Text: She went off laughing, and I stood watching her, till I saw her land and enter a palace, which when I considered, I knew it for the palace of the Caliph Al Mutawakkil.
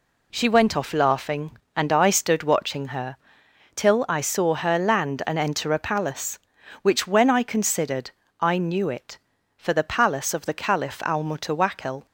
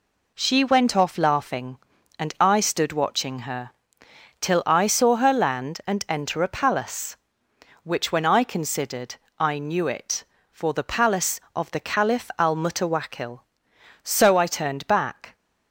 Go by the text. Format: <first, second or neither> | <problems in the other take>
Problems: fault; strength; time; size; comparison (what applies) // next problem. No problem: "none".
first | goes on to say "So I turned back"; noticeable; from 14.0 s on; 1.3 s long